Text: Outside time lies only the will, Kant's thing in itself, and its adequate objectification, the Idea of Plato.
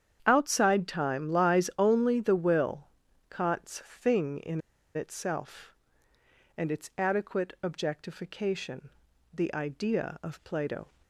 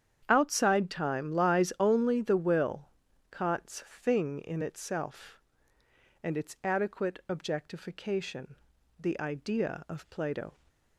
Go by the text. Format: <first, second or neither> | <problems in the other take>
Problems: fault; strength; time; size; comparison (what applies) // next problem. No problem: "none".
second | starts louder than the rest; strong; until 1.2 s; 8.5 dB; strong in the second // pauses between "in" and "itself"; slight; at 4.6 s; 0.34 s long